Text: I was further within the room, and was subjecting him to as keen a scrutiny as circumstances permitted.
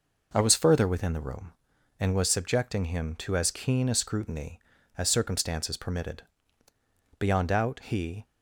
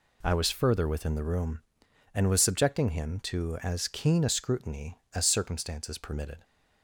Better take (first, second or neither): second